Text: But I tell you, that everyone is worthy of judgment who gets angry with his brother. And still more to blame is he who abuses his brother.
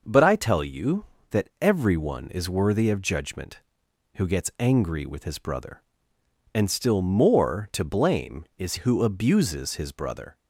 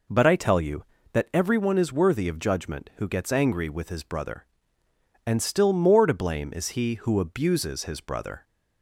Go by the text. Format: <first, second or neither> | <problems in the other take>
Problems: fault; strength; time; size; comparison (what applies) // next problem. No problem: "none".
second | skips "he"; at 8.7 s